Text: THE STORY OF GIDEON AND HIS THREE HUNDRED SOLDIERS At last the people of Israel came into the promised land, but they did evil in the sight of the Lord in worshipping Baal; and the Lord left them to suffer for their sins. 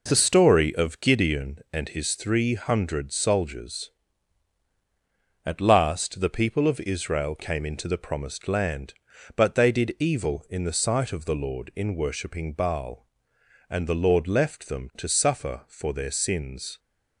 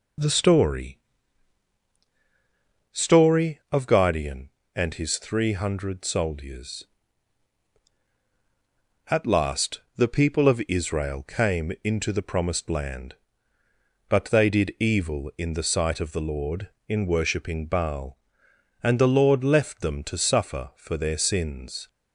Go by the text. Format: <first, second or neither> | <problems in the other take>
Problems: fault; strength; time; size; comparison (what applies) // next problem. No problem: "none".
first | says "STORY" twice; at 2.9 s // pauses between "last" and "the"; slight; at 9.7 s; 0.18 s long